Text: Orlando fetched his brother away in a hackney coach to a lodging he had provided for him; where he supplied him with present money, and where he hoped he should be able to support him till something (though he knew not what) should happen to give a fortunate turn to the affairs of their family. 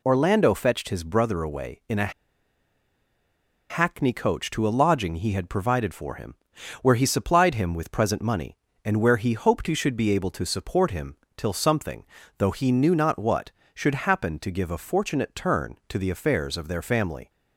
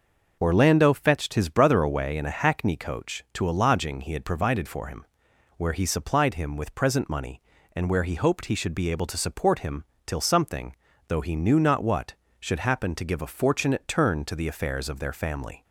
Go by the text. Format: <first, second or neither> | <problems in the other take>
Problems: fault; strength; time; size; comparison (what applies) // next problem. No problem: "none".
second | pauses between "a" and "hackney"; strong; at 2.1 s; 1.5 s long // pauses between "him" and "till"; slight; at 11.1 s; 0.18 s long; slight in the second